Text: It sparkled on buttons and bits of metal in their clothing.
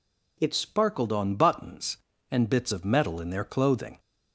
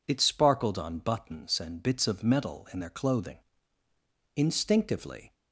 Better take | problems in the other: first | goes on to say "Instinctively"; noticeable; from 4.3 s on; 0.98 s long

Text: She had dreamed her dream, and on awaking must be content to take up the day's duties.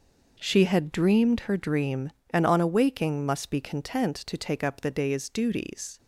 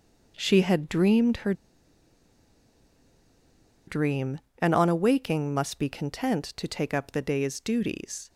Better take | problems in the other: first | pauses between "her" and "dream"; strong; at 1.5 s; 2.3 s long

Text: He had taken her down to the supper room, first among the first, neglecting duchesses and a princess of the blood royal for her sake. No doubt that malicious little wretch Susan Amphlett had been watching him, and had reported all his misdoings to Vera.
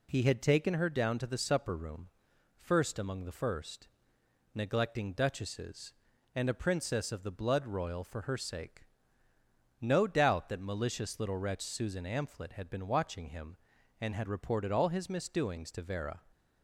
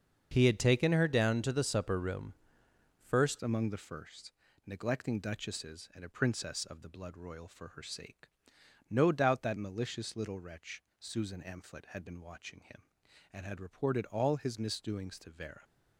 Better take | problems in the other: first | starts louder than the rest; until 1.3 s; 6.5 dB // changes voice at "among"; from 3.4 s on; 12.2 s long // pauses between "wretch" and "Susan"; slight; at 10.8 s; 0.18 s long

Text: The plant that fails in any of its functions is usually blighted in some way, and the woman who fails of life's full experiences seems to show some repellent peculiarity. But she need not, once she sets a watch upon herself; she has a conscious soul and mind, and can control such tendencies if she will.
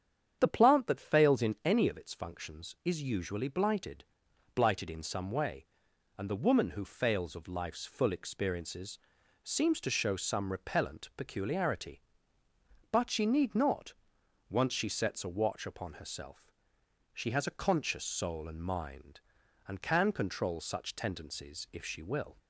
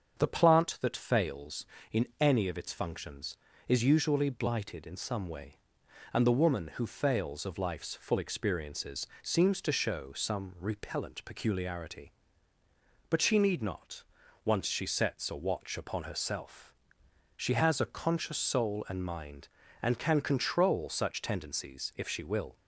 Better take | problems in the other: second | starts louder than the rest; strong; until 1.4 s; 8.5 dB; strong in the second // says "blighted" twice; at 4.5 s // pauses between "experiences" and "seems"; noticeable; at 8.9 s; 0.46 s long; slight in the second

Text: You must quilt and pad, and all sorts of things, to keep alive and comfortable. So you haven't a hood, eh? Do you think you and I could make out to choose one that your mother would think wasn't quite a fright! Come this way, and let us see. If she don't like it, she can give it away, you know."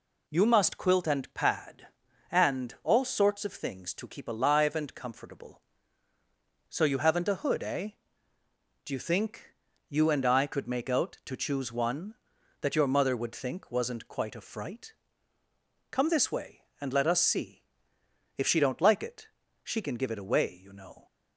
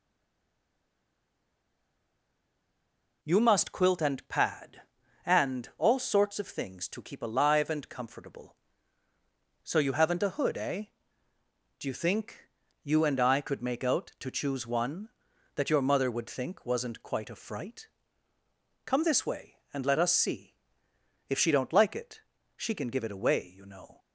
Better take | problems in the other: first | stays silent before the first word; strong; until 3.2 s; 3.2 s long // pauses between "think" and "you"; slight; at 12.4 s; 0.36 s long; slight in the first

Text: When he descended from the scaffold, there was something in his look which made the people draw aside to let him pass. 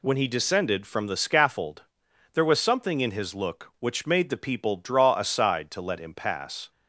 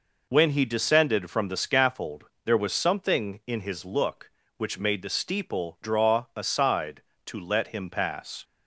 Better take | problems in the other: first | says "steeple" for "people"; at 5.0 s

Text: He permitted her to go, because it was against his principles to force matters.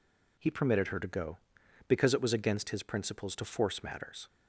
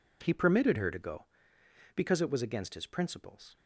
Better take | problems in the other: first | stops before "to force matters"; at 3.5 s

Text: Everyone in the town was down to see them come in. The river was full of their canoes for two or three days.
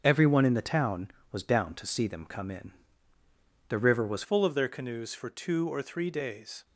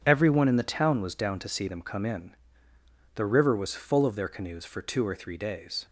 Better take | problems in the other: second | starts louder than the rest; until 1.0 s; 6.5 dB; strong in the second // changes voice at "full"; from 4.2 s on; 2.4 s long

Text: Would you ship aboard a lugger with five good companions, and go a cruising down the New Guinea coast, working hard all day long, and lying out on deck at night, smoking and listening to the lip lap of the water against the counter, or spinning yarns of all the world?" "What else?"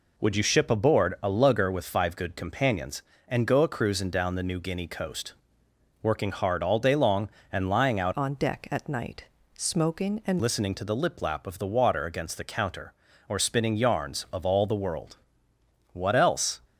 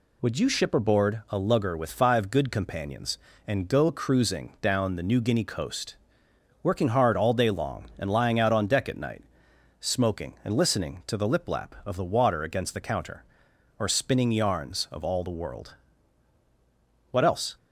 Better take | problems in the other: second | changes voice from "on" to "and"; from 8.1 to 10.4 s; 2.3 s long

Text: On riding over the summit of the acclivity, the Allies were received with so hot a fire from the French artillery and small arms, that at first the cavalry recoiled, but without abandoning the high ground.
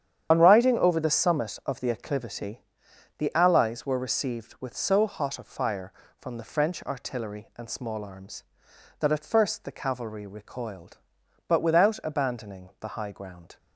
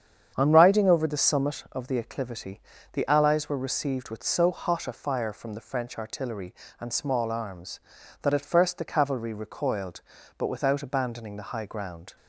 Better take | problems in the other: second | loses the start of "On"; at 0.3 s; 40 ms // starts louder than the rest; strong; until 1.3 s; 9 dB; strong in the second

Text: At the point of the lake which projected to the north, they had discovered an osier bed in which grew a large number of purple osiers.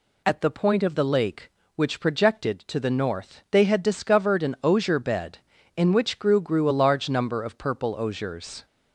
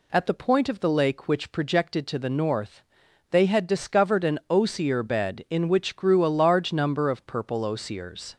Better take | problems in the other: second | says "grew" twice; at 6.3 s

